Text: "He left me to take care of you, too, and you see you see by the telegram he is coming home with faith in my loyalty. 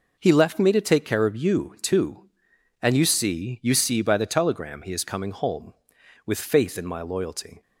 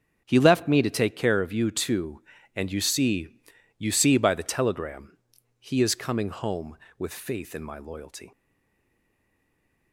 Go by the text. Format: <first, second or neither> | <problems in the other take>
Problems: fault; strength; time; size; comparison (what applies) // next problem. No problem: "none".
first | starts louder than the rest; until 1.2 s; 6.5 dB // pauses between "see" and "you"; at 3.3 s; 0.40 s long // pauses between "telegram" and "he"; at 5.1 s; 0.42 s long // stays silent after the last word; noticeable; from 8.3 s on; 1.6 s long